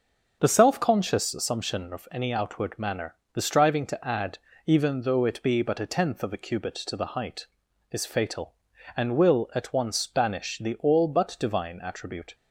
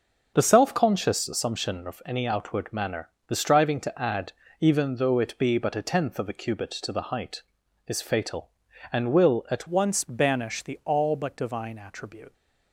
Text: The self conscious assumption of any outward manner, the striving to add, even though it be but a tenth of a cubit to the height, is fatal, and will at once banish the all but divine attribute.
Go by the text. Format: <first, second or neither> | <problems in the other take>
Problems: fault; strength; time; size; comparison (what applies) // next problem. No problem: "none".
first | starts louder than the rest; until 1.3 s; 6.5 dB; also in the first // changes voice at "once"; from 9.6 s on; 2.7 s long